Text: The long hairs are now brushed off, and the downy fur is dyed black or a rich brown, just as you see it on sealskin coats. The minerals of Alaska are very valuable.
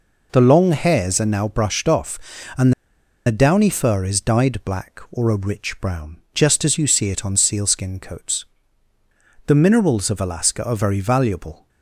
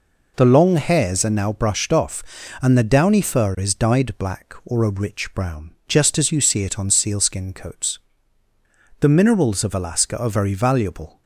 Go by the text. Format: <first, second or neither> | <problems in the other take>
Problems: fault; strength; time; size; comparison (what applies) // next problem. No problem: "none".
second | pauses between "and" and "the"; noticeable; at 2.7 s; 0.54 s long